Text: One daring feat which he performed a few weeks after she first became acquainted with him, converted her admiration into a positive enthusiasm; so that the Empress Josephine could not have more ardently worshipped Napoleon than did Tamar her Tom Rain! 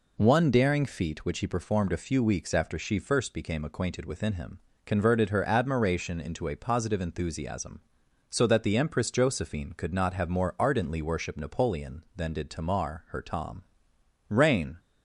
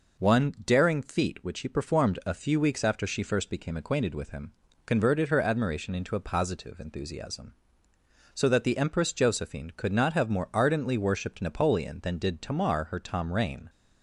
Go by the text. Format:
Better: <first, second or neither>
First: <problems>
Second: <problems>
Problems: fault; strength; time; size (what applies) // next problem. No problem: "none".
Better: second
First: says "within" for "with"; at 4.0 s // pauses between "Tom" and "Rain"; noticeable; at 13.6 s; 0.66 s long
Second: none